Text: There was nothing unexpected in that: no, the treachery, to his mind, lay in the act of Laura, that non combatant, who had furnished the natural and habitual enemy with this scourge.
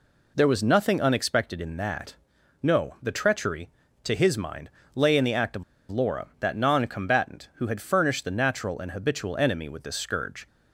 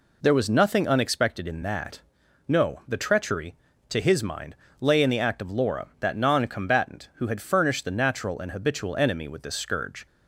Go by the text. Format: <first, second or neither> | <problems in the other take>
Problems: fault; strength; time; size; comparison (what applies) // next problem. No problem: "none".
second | pauses between "of" and "Laura"; slight; at 5.6 s; 0.26 s long